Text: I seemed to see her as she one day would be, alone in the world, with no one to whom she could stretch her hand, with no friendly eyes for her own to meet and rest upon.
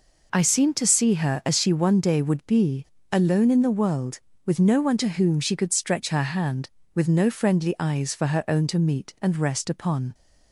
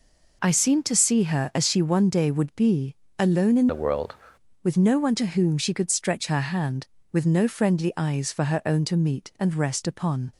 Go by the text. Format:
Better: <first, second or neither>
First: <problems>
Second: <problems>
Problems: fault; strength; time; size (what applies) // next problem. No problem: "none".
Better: first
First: none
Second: changes voice from "the" to "world"; from 3.6 to 4.1 s; 0.5 s long